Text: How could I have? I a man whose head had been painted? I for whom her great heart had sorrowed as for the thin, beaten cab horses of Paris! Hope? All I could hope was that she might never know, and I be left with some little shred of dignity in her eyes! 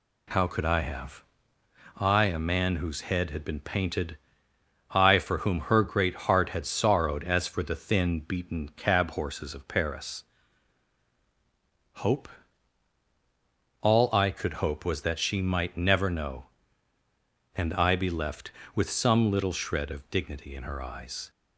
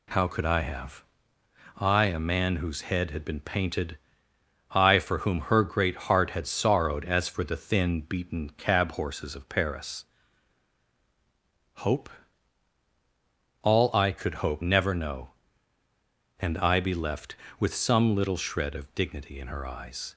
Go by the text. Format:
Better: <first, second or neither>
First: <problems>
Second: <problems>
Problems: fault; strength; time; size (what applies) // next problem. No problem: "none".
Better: first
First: none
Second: skips "was that she might"; at 14.6 s